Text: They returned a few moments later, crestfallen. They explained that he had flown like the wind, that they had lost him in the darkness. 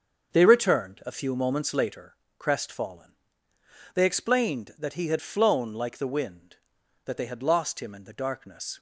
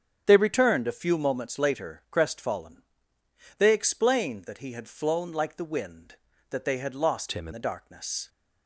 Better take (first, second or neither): first